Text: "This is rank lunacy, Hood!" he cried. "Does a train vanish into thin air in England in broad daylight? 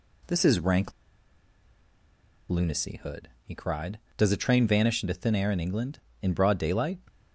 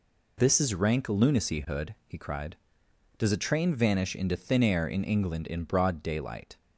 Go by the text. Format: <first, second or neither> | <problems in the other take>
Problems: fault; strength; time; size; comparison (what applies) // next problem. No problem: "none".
second | pauses between "rank" and "lunacy"; strong; at 0.9 s; 1.5 s long